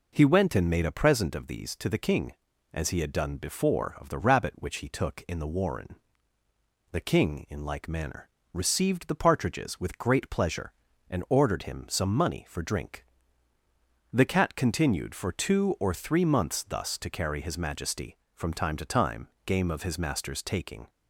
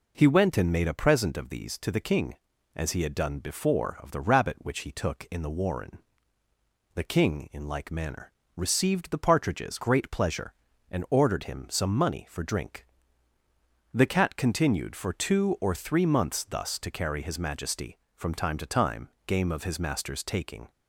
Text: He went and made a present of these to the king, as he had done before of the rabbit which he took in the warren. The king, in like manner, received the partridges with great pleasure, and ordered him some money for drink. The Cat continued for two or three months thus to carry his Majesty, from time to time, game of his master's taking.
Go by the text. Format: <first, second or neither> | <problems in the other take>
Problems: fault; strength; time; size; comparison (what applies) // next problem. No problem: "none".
first | skips "with"; at 9.8 s